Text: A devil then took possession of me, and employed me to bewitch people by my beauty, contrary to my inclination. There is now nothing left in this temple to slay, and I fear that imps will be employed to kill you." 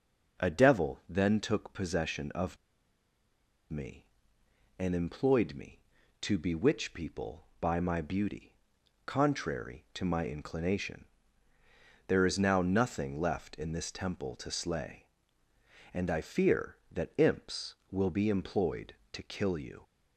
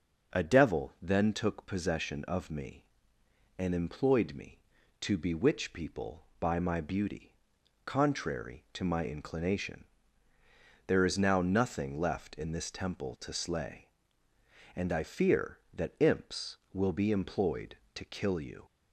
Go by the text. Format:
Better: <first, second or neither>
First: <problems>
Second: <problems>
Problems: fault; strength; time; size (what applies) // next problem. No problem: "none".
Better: second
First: pauses between "of" and "me"; at 2.5 s; 1.1 s long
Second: none